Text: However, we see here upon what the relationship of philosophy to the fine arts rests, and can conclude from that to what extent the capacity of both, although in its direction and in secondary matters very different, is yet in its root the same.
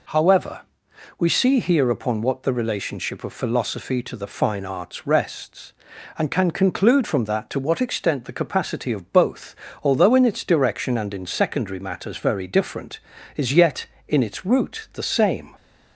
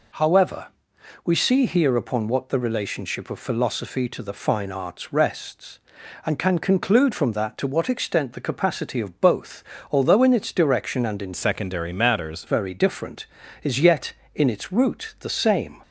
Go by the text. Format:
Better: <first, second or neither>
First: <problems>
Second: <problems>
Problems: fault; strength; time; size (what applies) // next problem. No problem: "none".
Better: first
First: none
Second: changes voice from "secondary" to "matters"; from 11.3 to 12.4 s; 1.1 s long